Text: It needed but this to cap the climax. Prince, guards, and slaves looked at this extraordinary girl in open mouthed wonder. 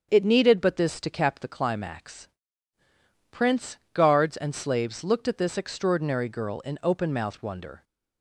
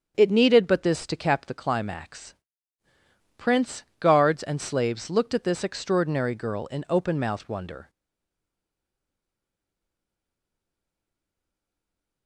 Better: first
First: starts louder than the rest; strong; until 1.1 s; 7.5 dB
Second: starts louder than the rest; strong; until 1.1 s; 7.5 dB // stays silent after the last word; strong; from 7.8 s on; 4.4 s long

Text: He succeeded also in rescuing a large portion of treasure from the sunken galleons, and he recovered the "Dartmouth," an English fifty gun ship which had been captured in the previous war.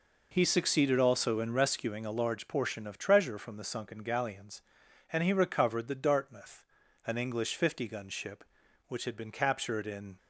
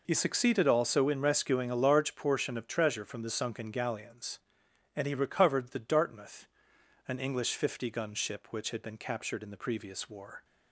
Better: second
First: stops before "the previous war"; at 10.1 s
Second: none

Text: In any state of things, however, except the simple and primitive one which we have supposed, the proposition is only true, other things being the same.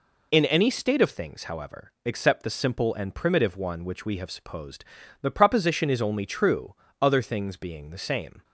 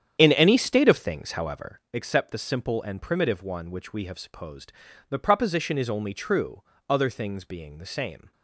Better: first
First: none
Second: starts louder than the rest; strong; until 2.0 s; 9 dB

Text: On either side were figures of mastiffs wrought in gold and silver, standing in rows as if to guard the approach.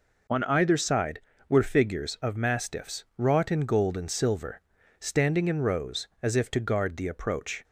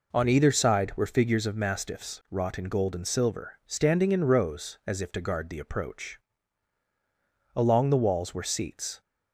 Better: first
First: none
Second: goes on to say "Along the walls were seats"; from 7.5 s on; 1.4 s long

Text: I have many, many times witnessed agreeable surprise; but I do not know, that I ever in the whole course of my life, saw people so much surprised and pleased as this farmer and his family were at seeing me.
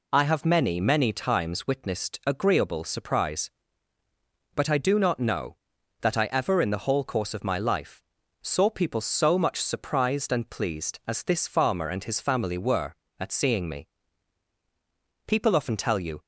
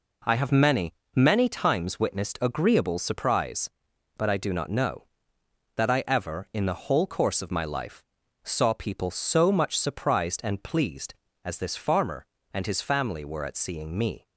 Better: second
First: goes on to say "People often tell you"; noticeable; from 15.2 s on; 0.96 s long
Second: none

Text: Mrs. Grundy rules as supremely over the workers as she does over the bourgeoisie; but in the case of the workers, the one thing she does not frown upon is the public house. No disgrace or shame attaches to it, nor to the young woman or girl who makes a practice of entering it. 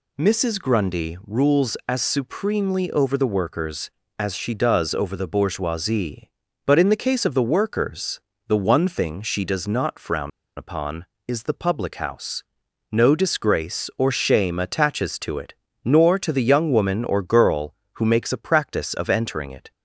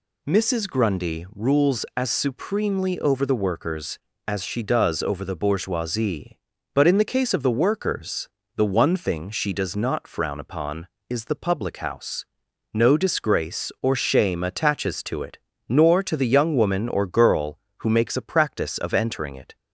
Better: second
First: pauses between "frown" and "upon"; slight; at 10.3 s; 0.26 s long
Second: none

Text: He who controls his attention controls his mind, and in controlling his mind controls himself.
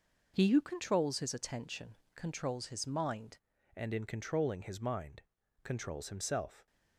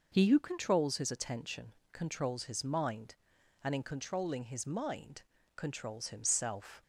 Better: second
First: pauses between "attention" and "controls"; slight; at 1.9 s; 0.20 s long // changes voice at "and"; from 3.7 s on; 2.9 s long // pauses between "mind" and "controls"; at 5.2 s; 0.40 s long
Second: pauses between "attention" and "controls"; slight; at 1.7 s; 0.20 s long // pauses between "mind" and "controls"; slight; at 5.2 s; 0.34 s long

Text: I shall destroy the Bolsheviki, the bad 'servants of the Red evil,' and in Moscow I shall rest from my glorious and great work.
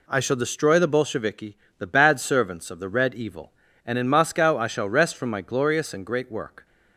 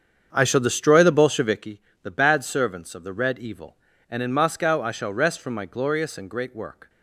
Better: first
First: none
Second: starts louder than the rest; strong; until 1.8 s; 7.5 dB

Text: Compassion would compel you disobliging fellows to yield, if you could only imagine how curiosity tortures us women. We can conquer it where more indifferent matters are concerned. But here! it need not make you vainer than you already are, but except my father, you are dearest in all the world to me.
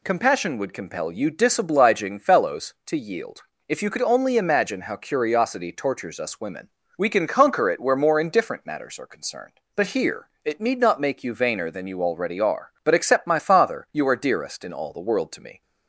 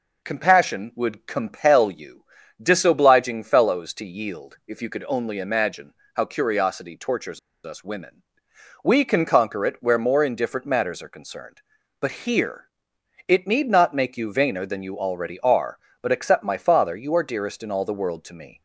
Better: first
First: none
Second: pauses between "you" and "disobliging"; at 2.2 s; 0.38 s long // pauses between "imagine" and "how"; slight; at 5.9 s; 0.20 s long // pauses between "tortures" and "us"; slight; at 7.3 s; 0.25 s long

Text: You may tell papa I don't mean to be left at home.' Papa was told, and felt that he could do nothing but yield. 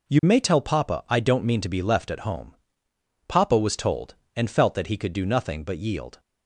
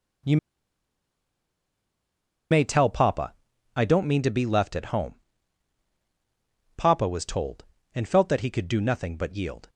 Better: first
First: none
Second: pauses between "You" and "may"; strong; at 0.3 s; 2.1 s long // pauses between "papa" and "I"; at 3.3 s; 0.44 s long

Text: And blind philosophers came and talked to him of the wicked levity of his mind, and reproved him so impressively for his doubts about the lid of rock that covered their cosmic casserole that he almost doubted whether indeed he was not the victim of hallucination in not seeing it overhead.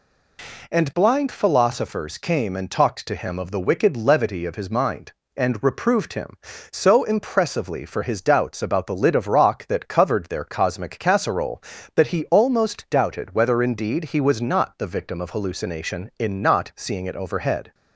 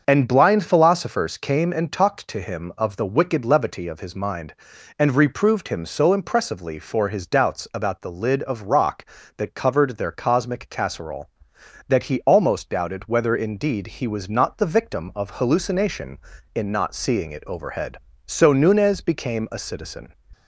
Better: first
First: none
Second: starts louder than the rest; until 1.1 s; 7 dB // goes on to say "So Nunez became a citizen"; strong; from 18.2 s on; 1.8 s long

